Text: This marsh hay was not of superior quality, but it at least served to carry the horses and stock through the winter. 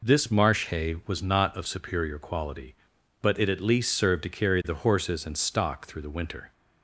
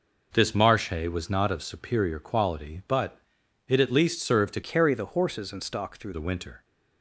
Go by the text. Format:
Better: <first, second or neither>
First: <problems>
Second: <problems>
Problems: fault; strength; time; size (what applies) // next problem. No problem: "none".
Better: first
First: none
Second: pauses between "but" and "it"; noticeable; at 3.1 s; 0.48 s long // changes voice from "carry" to "through"; from 4.6 to 6.1 s; 1.5 s long